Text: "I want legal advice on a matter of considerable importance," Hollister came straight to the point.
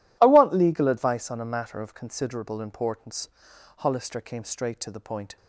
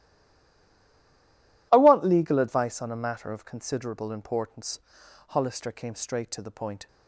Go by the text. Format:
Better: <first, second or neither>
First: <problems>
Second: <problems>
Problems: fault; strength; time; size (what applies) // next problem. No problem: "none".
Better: first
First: none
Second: stays silent before the first word; noticeable; until 1.7 s; 1.7 s long